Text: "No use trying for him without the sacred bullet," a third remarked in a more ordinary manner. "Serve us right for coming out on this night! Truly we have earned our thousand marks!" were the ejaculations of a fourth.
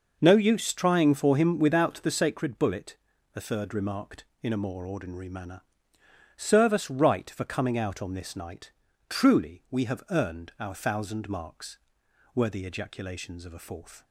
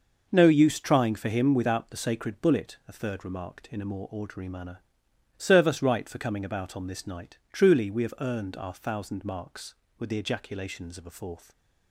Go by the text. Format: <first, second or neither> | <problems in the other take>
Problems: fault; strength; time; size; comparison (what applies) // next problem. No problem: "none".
first | says "about" for "out"; at 6.4 s